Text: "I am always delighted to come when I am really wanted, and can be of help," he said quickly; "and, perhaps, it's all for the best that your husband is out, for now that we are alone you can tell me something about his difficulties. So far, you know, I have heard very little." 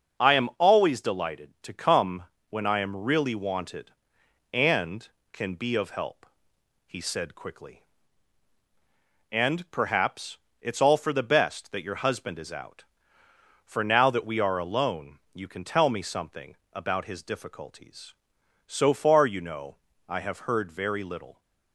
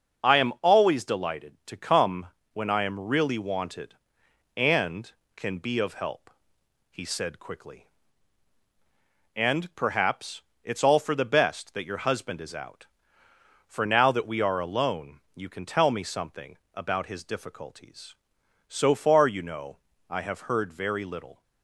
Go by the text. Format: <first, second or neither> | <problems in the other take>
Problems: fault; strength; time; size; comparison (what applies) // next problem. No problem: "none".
neither | starts louder than the rest; the same in both // pauses between "come" and "when"; slight; the same in both // pauses between "something" and "about"; slight; the same in both